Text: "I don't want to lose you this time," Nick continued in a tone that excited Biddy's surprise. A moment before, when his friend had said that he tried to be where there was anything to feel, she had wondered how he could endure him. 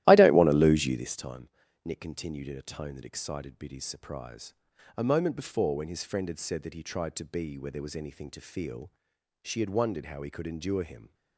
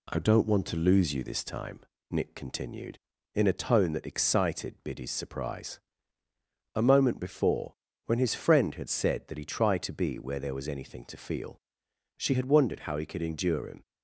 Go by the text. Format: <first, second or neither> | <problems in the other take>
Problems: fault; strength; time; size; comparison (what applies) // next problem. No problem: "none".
second | starts louder than the rest; strong; until 1.1 s; 15 dB